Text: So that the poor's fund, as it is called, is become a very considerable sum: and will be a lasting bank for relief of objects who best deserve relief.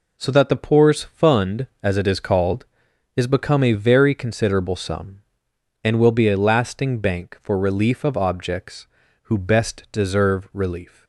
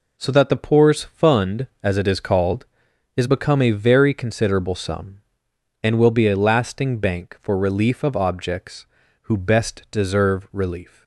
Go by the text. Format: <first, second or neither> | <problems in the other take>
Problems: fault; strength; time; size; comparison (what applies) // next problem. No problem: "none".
neither | none